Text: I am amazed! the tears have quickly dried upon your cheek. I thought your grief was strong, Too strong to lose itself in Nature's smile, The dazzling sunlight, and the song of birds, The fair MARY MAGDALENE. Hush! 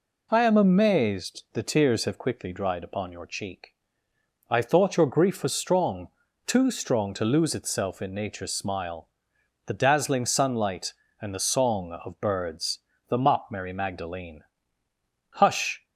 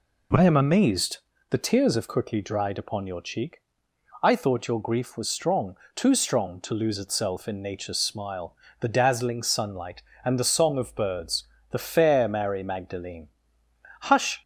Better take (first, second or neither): second